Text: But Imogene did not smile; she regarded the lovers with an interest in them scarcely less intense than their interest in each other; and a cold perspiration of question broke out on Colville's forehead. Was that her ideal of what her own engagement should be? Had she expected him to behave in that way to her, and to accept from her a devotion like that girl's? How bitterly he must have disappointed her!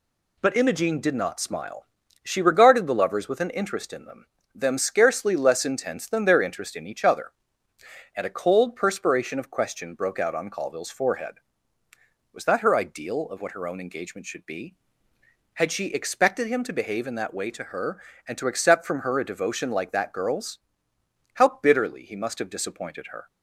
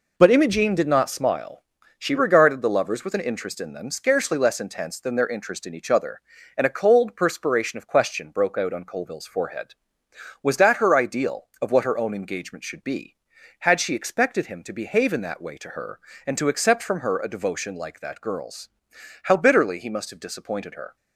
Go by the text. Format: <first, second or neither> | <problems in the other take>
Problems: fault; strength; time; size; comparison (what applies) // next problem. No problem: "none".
second | says "them" twice; at 4.5 s